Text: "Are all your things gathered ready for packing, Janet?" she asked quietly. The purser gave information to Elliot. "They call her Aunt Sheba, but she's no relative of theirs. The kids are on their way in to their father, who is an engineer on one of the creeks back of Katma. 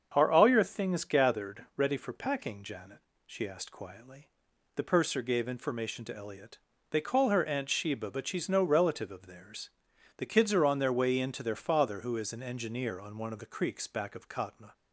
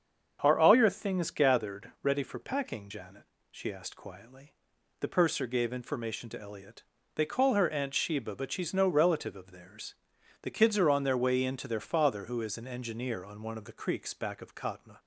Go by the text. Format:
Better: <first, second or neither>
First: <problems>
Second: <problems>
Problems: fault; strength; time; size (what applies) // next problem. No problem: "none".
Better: neither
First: starts louder than the rest; until 1.1 s; 7 dB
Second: starts louder than the rest; strong; until 1.4 s; 7 dB